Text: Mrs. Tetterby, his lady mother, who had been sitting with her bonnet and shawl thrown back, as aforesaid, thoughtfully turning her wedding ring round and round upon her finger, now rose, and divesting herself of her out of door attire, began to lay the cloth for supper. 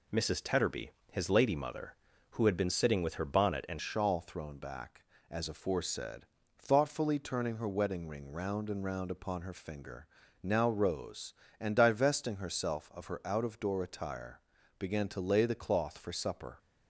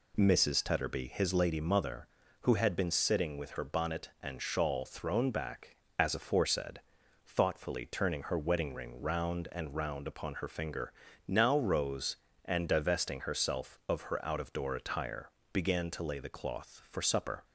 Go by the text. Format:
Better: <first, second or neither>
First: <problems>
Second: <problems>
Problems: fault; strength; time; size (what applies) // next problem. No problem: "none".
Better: second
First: changes voice at "shawl"; from 3.7 s on; 12.8 s long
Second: none